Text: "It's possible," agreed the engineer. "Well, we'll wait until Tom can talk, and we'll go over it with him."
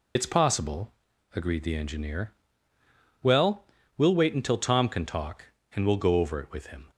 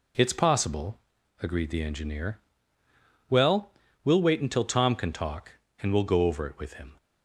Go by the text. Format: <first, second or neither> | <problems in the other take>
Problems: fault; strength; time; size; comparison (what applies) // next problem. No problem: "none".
second | loses the start of "It's"; at 0.1 s; 70 ms